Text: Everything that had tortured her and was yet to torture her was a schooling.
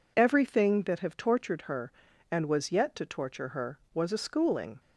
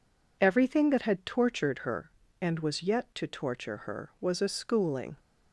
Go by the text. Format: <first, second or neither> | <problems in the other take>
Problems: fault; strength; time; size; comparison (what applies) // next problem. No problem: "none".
second | says "have" for "had"; at 0.9 s